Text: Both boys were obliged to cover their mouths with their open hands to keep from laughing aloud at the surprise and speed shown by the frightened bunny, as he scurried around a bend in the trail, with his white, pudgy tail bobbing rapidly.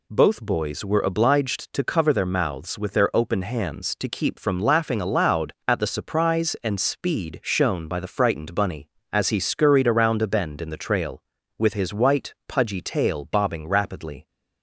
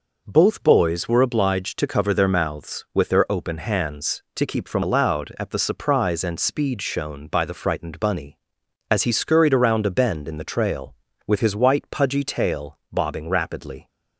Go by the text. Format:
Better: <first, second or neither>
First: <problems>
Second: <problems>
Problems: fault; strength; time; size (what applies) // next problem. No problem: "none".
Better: first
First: none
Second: skips "laughing"; at 4.8 s